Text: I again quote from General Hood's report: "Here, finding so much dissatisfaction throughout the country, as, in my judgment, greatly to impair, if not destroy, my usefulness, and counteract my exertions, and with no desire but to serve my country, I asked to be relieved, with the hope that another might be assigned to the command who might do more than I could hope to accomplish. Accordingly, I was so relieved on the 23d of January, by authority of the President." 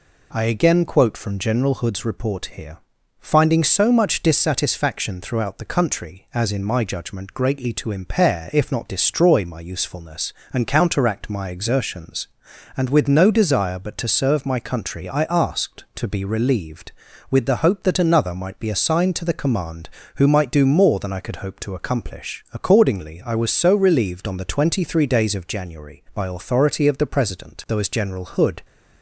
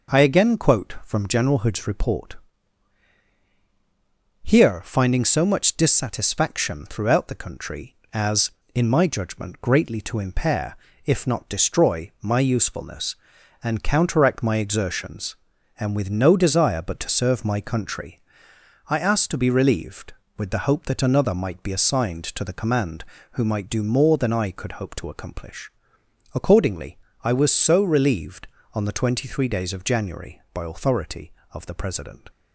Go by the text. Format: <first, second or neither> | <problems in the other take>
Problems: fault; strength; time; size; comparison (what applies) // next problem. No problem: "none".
second | goes on to say "Though as General Hood"; noticeable; from 27.6 s on; 0.94 s long